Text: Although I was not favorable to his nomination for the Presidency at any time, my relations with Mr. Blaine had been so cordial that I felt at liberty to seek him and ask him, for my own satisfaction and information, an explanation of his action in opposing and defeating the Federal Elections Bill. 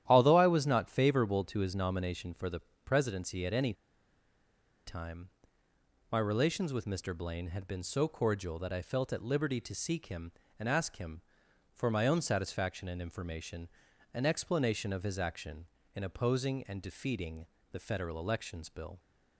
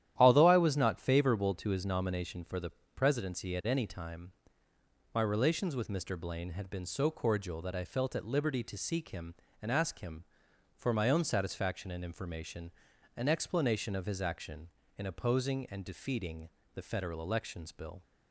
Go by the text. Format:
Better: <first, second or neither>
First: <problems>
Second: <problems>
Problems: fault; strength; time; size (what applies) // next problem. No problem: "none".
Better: second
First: starts louder than the rest; strong; until 1.0 s; 11.5 dB // pauses between "the" and "Presidency"; slight; at 2.6 s; 0.24 s long // pauses between "any" and "time"; at 3.7 s; 1.1 s long // pauses between "defeating" and "the"; slight; at 17.4 s; 0.24 s long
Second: starts louder than the rest; strong; until 1.1 s; 11.5 dB // pauses between "the" and "Presidency"; slight; at 2.7 s; 0.24 s long // pauses between "defeating" and "the"; slight; at 16.4 s; 0.24 s long